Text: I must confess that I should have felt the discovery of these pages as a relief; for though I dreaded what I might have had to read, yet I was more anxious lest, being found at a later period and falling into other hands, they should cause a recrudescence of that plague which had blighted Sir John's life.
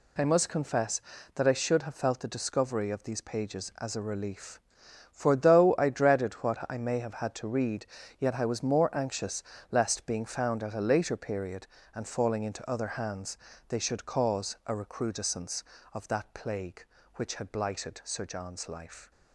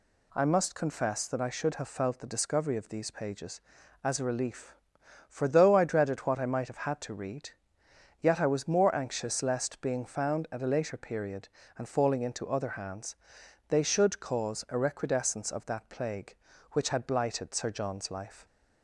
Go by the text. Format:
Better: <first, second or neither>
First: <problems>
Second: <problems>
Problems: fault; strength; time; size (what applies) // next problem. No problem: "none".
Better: second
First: says "may" for "might"; at 6.7 s // pauses between "anxious" and "lest"; slight; at 9.4 s; 0.28 s long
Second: none